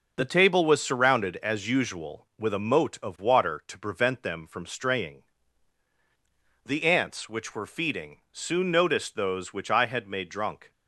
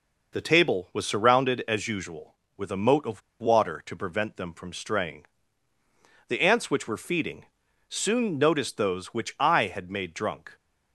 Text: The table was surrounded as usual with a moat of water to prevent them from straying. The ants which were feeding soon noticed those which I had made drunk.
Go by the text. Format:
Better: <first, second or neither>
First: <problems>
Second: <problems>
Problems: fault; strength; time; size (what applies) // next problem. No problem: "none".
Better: first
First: none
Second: pauses between "of" and "water"; slight; at 3.2 s; 0.20 s long // pauses between "feeding" and "soon"; at 7.4 s; 0.44 s long